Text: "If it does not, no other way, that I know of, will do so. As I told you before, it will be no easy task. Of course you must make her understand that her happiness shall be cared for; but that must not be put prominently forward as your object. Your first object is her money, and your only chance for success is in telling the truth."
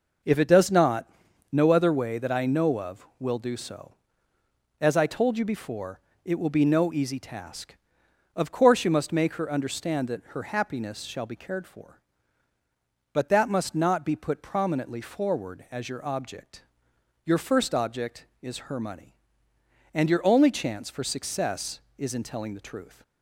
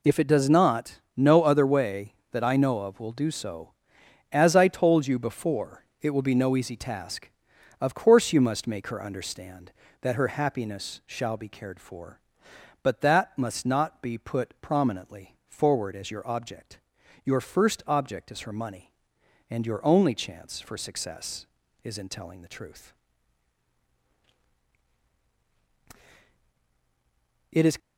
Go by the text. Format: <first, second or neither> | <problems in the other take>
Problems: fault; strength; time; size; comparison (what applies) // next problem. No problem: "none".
first | goes on to say "It is"; slight; from 27.5 s on; 0.26 s long